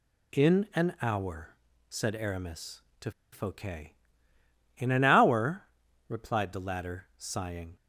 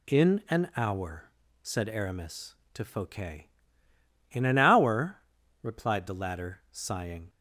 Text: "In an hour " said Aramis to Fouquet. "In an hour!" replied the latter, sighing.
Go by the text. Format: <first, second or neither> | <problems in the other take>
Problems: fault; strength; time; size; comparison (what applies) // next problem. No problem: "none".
second | pauses between "to" and "Fouquet"; slight; at 3.1 s; 0.22 s long